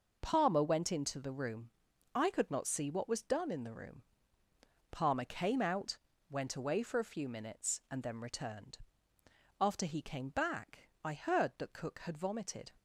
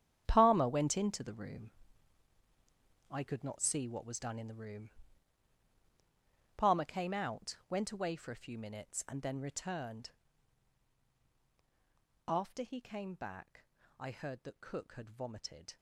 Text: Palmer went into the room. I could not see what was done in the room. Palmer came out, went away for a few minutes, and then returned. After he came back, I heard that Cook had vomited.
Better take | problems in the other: first | gets quieter; strong; throughout; 14 dB

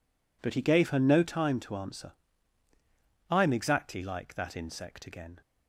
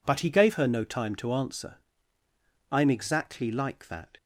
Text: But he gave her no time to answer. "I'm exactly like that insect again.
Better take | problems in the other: first | stops before "insect again"; at 4.1 s

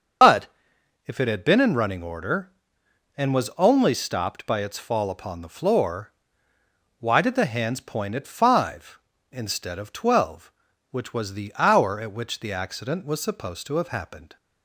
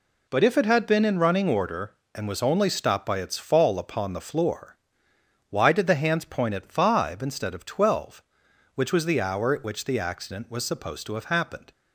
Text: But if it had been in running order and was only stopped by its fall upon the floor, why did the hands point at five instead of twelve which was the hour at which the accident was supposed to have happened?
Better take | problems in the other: second | loses the start of "But"; at 0.2 s; 90 ms // starts louder than the rest; until 1.8 s; 6.5 dB // pauses between "But" and "if"; noticeable; at 0.4 s; 0.60 s long

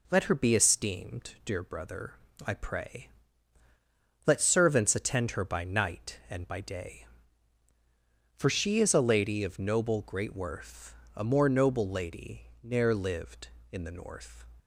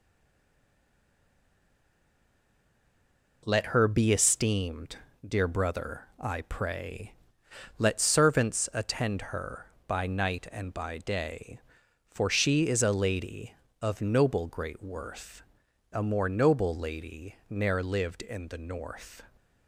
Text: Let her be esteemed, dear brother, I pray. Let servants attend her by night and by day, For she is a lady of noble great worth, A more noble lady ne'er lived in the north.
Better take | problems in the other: first | stays silent before the first word; strong; until 3.4 s; 3.4 s long

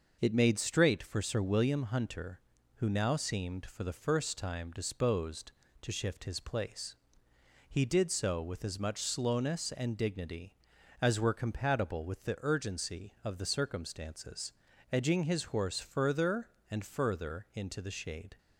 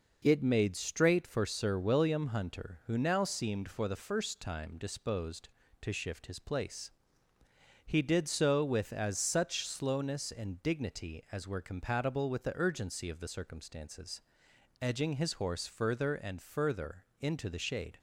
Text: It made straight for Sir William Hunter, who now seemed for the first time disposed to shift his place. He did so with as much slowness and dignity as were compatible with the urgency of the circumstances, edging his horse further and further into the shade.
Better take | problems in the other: first | says "such" for "much"; at 9.1 s // pauses between "further" and "into"; slight; at 17.0 s; 0.18 s long

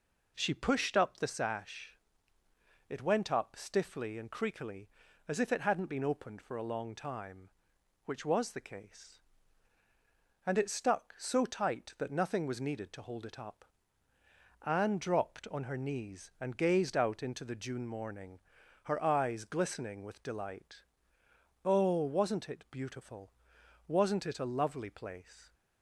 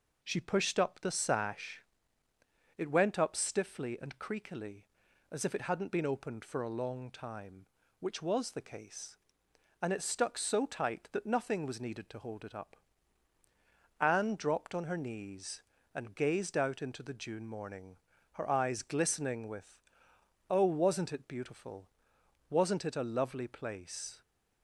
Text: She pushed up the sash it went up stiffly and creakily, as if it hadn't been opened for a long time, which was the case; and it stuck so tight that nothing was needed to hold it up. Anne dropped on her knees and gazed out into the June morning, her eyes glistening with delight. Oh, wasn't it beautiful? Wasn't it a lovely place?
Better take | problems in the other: first | pauses between "sash" and "it"; noticeable; at 1.8 s; 0.96 s long; noticeable in the first // skips "delight"; at 20.1 s

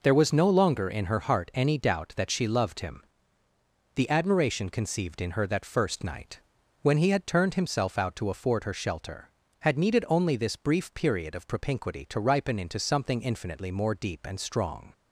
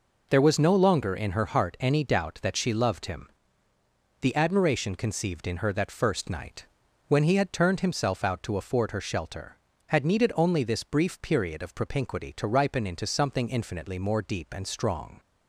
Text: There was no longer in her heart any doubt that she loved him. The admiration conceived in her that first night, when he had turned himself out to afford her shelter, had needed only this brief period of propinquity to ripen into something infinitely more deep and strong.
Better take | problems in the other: neither | none

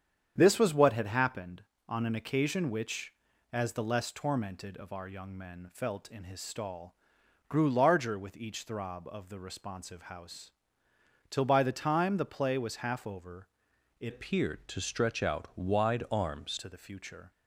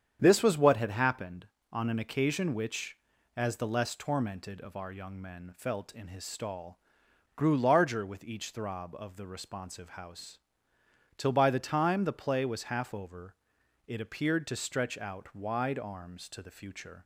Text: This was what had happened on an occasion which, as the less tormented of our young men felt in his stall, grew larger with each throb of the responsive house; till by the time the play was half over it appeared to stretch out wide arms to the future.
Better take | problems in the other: second | starts louder than the rest; strong; until 1.3 s; 8.5 dB; strong in the second // pauses between "over" and "it"; noticeable; at 13.4 s; 0.52 s long; noticeable in the second // changes voice from "appeared" to "arms"; from 14.0 to 16.5 s; 2.5 s long

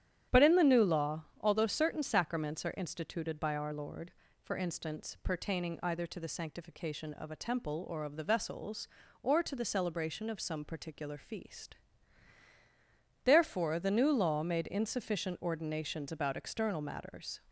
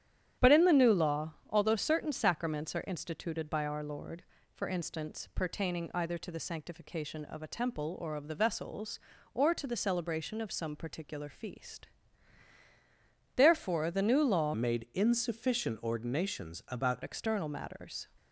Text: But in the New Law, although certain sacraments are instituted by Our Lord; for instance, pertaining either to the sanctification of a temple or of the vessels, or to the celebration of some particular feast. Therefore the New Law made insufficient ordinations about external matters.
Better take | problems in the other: first | starts louder than the rest; strong; until 1.5 s; 10 dB; strong in the first // changes voice from "made" to "about"; from 14.5 to 17.0 s; 2.5 s long

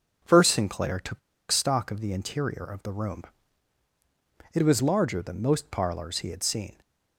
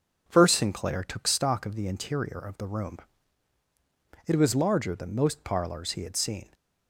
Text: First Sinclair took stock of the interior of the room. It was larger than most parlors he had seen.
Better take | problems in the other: second | pauses between "took" and "stock"; slight; at 1.1 s; 0.30 s long

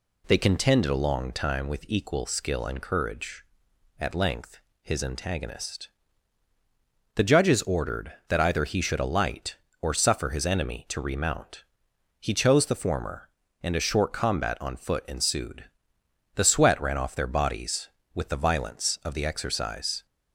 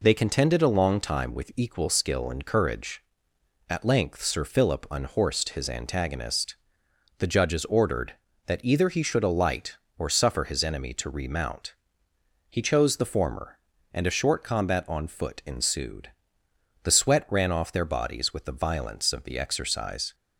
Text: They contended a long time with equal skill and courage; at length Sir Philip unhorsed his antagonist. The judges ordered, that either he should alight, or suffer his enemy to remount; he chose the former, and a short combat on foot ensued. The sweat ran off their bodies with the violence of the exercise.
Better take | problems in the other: second | skips "Sir Philip unhorsed"; at 4.7 s

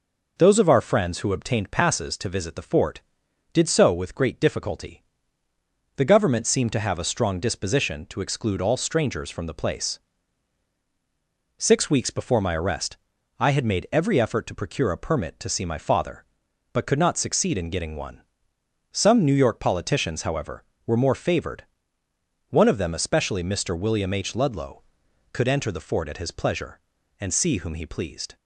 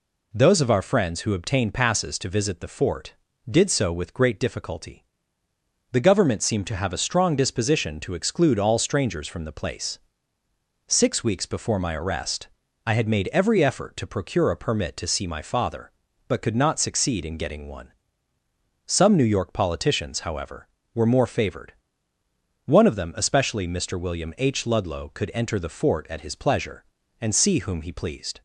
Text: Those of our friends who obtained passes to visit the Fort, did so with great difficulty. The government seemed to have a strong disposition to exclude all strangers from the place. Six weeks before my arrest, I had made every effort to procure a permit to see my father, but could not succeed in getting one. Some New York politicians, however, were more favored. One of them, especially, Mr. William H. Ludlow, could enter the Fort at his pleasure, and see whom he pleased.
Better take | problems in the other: neither | none

